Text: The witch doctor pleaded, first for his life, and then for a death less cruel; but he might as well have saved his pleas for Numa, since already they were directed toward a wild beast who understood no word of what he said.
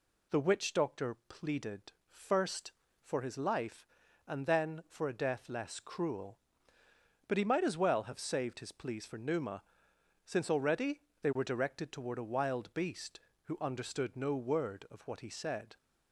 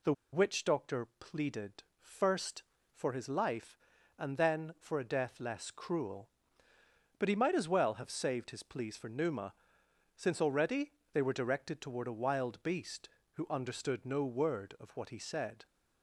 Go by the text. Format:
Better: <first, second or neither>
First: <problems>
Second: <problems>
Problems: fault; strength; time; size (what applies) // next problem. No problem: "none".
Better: first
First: pauses between "already" and "they"; slight; at 11.0 s; 0.20 s long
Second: pauses between "The" and "witch"; slight; at 0.1 s; 0.20 s long // pauses between "already" and "they"; slight; at 10.9 s; 0.20 s long